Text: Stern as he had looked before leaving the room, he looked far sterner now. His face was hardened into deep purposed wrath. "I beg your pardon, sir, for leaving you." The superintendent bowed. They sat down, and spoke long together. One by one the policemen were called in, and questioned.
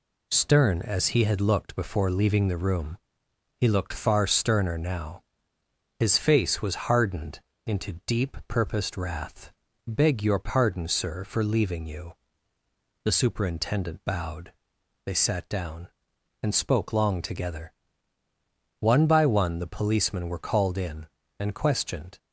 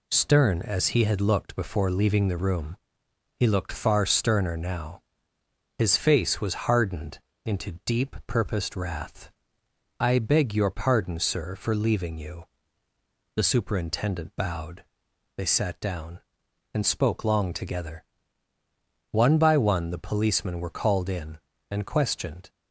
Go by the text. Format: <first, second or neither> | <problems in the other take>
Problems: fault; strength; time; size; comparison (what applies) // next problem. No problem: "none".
second | pauses between "hardened" and "into"; slight; at 7.4 s; 0.24 s long; slight in the second // skips "I"; at 9.6 s